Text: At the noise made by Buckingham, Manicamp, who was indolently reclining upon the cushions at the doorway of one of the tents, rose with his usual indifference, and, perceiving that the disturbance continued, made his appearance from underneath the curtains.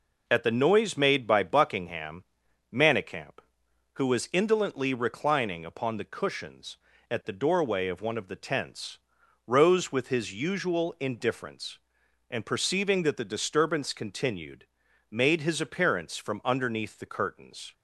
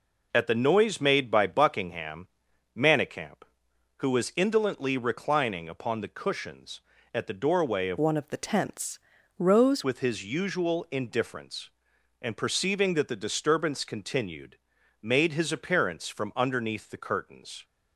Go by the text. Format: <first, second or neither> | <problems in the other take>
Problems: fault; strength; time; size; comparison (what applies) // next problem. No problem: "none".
first | changes voice from "one" to "rose"; from 7.9 to 9.8 s; 1.9 s long